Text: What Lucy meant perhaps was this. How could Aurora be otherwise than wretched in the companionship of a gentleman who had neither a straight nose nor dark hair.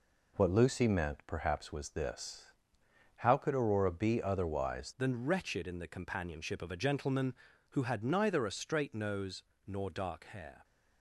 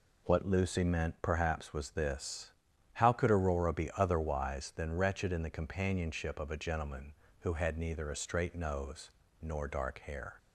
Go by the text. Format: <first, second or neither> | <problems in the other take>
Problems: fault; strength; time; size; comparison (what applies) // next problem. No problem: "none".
second | changes voice at "than"; from 4.9 s on; 5.7 s long // pauses between "nose" and "nor"; slight; at 9.4 s; 0.22 s long; slight in the second